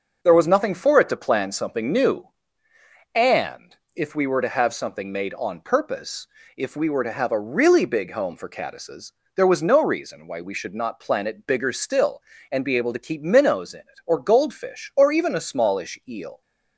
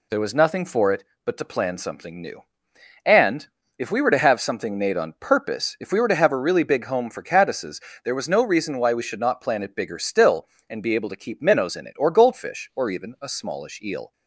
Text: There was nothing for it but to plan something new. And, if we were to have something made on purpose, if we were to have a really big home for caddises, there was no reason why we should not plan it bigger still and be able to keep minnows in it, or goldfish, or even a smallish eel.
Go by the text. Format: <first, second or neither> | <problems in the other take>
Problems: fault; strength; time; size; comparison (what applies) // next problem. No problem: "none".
second | skips "but"; at 1.0 s